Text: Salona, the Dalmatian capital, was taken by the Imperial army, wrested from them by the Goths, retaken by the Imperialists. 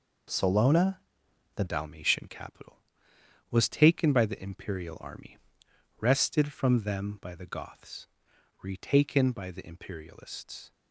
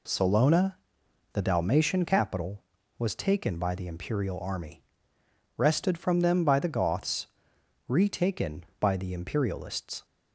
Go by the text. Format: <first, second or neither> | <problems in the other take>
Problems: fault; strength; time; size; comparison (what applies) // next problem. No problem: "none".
second | changes voice at "Dalmatian"; from 1.6 s on; 9.1 s long